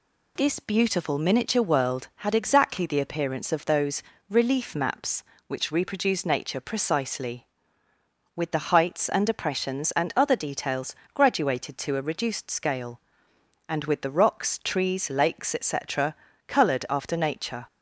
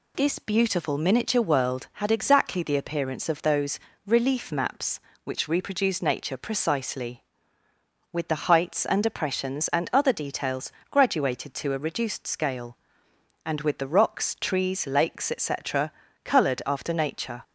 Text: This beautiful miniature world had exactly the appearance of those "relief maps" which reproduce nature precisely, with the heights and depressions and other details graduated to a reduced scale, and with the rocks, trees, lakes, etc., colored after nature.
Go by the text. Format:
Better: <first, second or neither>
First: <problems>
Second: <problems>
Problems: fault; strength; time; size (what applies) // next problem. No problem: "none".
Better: neither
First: pauses between "those" and "relief"; slight; at 4.0 s; 0.26 s long // pauses between "details" and "graduated"; slight; at 10.9 s; 0.18 s long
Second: pauses between "those" and "relief"; slight; at 3.8 s; 0.26 s long // pauses between "details" and "graduated"; slight; at 10.7 s; 0.18 s long